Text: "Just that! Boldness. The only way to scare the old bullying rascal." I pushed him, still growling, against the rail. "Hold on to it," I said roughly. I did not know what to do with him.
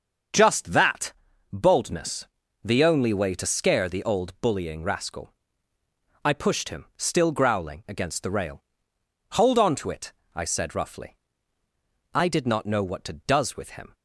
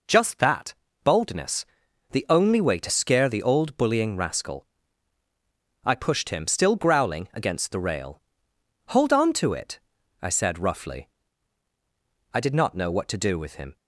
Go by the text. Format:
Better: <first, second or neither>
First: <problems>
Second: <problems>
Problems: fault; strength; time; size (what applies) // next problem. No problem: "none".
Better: second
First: starts louder than the rest; until 1.7 s; 6.5 dB // says "does" for "do"; at 13.1 s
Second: none